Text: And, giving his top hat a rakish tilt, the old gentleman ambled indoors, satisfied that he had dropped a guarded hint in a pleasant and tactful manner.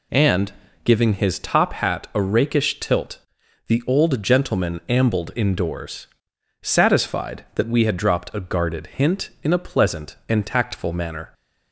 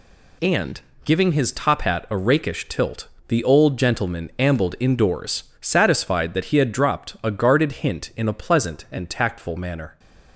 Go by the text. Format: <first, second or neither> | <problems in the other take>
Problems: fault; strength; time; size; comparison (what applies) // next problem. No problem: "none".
second | says "we" for "he"; at 7.6 s